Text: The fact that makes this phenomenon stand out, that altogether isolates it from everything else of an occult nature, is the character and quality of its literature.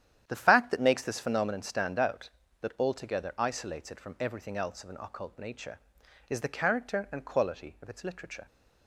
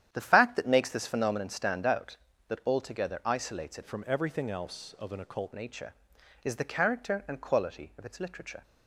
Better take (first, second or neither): first